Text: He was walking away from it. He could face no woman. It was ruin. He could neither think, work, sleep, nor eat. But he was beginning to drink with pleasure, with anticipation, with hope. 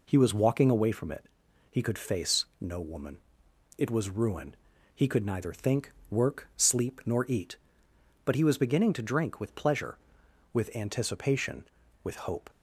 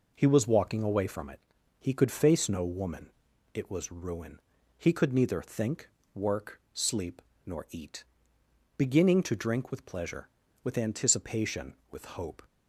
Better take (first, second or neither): first